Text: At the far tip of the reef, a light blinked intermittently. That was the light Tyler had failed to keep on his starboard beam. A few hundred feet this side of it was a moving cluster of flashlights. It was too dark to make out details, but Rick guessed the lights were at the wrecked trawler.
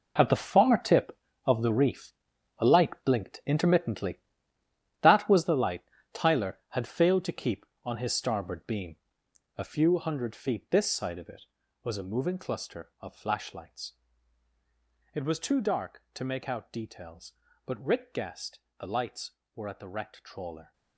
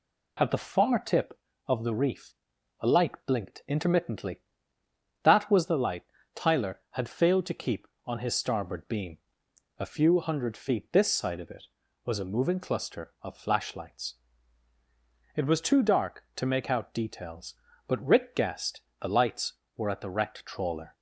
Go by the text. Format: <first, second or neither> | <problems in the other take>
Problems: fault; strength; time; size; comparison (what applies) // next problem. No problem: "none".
second | gets quieter; strong; throughout; 12.5 dB // pauses between "light" and "Tyler"; slight; at 5.8 s; 0.32 s long; slight in the second // pauses between "guessed" and "the"; slight; at 18.6 s; 0.20 s long; slight in the second